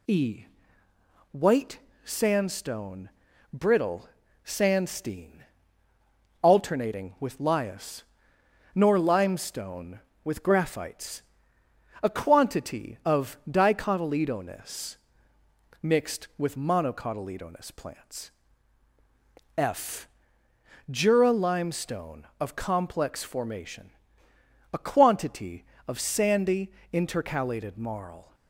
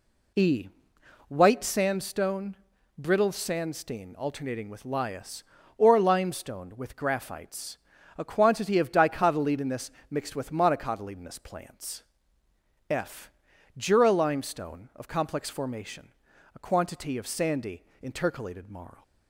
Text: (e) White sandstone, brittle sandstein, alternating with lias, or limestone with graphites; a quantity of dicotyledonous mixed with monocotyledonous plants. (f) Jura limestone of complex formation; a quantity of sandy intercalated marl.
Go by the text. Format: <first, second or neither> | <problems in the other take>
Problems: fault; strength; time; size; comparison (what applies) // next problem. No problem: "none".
second | pauses between "White" and "sandstone"; slight; at 1.7 s; 0.24 s long // pauses between "brittle" and "sandstein"; at 4.0 s; 0.38 s long // says "nor" for "or"; at 8.7 s // pauses between "dicotyledonous" and "mixed"; noticeable; at 14.9 s; 0.84 s long; slight in the second // pauses between "sandy" and "intercalated"; slight; at 26.7 s; 0.22 s long; slight in the second